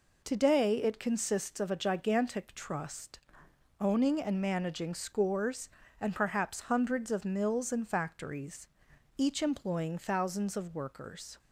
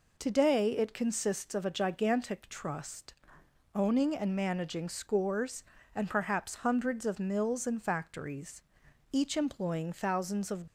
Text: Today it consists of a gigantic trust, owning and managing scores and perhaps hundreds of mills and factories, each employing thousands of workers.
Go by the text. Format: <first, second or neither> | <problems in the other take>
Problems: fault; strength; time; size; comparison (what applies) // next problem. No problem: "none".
first | stops before "workers"; at 10.6 s